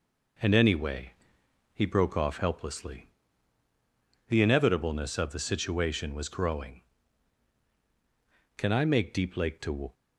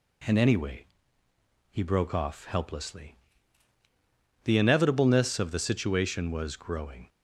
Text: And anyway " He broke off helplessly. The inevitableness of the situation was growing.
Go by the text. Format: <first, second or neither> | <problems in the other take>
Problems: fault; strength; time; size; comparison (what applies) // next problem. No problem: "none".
second | goes on to say "Can I make Deep Lake to"; from 8.5 s on; 1.3 s long